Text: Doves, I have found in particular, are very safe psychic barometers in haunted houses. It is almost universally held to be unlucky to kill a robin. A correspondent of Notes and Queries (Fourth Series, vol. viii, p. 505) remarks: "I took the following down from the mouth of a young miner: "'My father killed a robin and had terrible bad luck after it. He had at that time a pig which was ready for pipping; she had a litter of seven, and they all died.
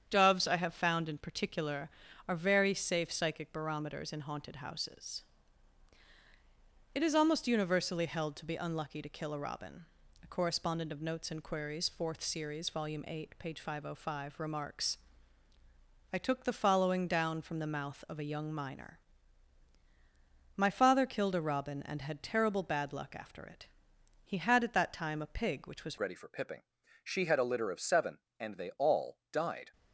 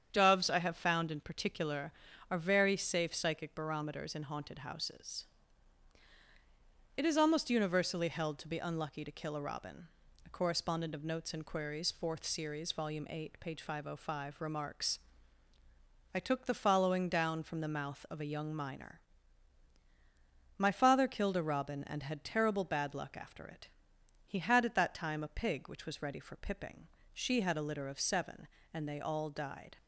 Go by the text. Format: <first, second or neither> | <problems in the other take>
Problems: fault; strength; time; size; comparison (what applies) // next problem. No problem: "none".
second | starts louder than the rest; strong; until 1.1 s; 8 dB; strong in the second // changes voice at "ready"; from 25.9 s on; 3.8 s long